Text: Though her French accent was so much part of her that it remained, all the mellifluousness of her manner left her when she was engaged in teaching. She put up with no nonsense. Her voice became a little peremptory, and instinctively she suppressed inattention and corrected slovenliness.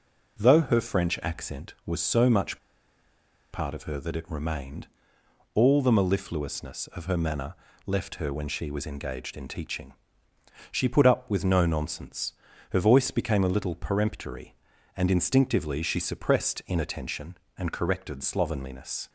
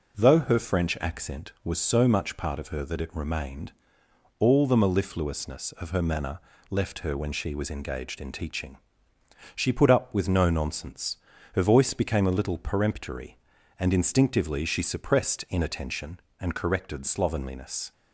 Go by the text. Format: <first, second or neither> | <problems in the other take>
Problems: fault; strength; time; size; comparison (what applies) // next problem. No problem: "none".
second | pauses between "much" and "part"; noticeable; at 2.5 s; 0.94 s long // pauses between "manner" and "left"; slight; at 7.5 s; 0.32 s long; slight in the second